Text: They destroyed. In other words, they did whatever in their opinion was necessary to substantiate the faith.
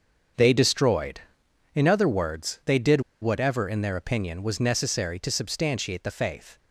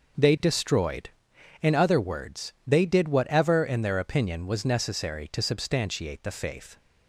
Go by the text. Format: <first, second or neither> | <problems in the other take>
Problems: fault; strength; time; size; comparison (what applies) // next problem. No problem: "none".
second | starts louder than the rest; until 1.9 s; 7 dB; noticeable in the second // pauses between "did" and "whatever"; slight; at 3.0 s; 0.21 s long